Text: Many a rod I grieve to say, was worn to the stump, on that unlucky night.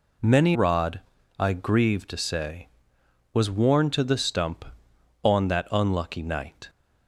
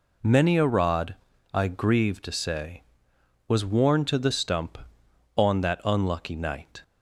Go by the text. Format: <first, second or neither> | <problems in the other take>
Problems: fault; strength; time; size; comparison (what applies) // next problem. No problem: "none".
second | skips "a"; at 0.5 s // pauses between "rod" and "I"; at 0.9 s; 0.40 s long; also in the second